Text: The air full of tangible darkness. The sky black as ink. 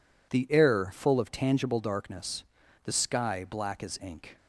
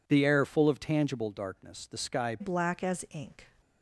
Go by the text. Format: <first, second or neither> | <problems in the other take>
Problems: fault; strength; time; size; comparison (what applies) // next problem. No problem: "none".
first | changes voice at "black"; from 2.4 s on; 1.1 s long